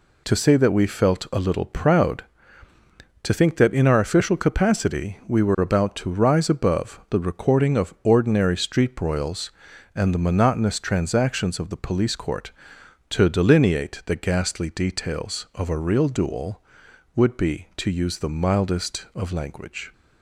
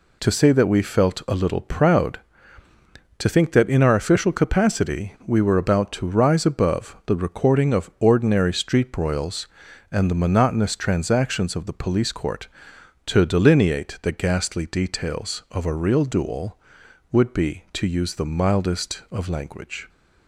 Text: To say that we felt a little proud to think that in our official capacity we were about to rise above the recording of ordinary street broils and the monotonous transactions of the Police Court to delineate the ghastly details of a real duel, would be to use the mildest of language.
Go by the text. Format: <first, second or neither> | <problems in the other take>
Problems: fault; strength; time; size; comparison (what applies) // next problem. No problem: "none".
neither | none